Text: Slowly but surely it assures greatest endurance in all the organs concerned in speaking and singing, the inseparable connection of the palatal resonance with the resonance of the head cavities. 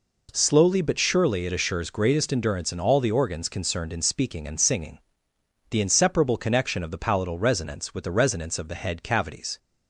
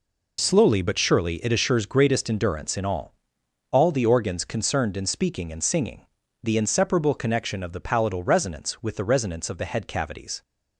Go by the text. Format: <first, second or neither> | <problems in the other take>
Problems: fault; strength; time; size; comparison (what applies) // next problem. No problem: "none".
first | says "all" twice; at 3.7 s